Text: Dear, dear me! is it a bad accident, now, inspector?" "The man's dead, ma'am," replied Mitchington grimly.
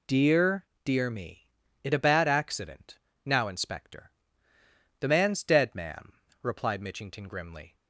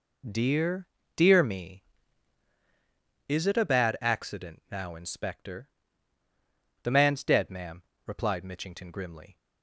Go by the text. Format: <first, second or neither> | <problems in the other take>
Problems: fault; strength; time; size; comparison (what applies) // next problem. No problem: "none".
second | skips "is"; at 1.6 s